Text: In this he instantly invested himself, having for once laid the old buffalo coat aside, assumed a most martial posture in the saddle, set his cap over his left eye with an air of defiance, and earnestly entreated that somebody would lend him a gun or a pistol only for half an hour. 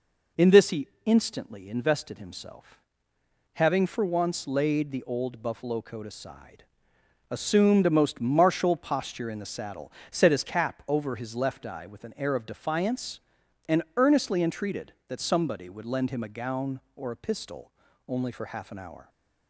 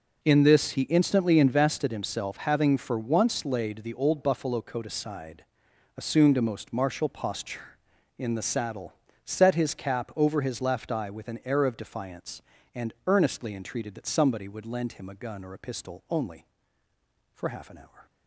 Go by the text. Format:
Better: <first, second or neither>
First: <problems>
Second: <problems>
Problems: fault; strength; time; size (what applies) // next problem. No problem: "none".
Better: second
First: pauses between "he" and "instantly"; slight; at 0.8 s; 0.18 s long // pauses between "and" and "earnestly"; slight; at 13.8 s; 0.16 s long // says "gown" for "gun"; at 16.2 s // pauses between "pistol" and "only"; slight; at 17.7 s; 0.36 s long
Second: none